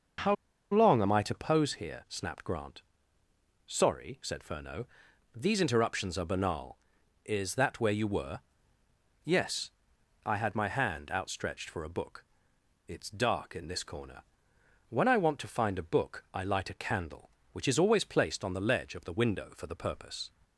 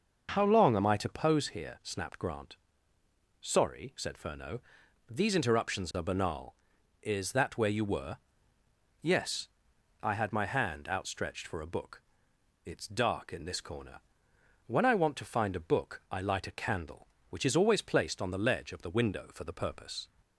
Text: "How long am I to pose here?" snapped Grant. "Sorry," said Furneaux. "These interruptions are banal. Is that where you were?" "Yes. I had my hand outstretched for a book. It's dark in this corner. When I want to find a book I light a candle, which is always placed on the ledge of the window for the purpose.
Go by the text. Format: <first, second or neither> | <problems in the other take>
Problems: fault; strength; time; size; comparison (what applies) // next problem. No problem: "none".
second | starts louder than the rest; until 1.6 s; 6 dB; also in the second // pauses between "How" and "long"; at 0.3 s; 0.36 s long